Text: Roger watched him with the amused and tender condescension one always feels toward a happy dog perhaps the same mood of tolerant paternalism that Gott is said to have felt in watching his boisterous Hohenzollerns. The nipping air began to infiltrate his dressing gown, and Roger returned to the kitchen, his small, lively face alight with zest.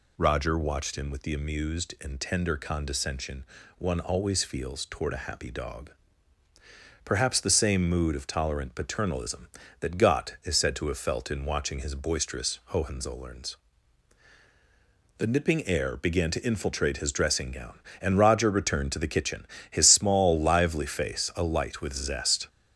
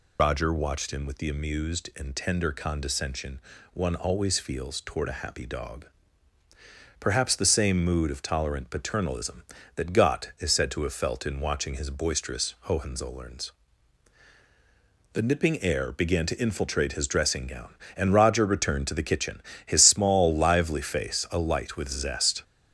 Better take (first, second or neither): first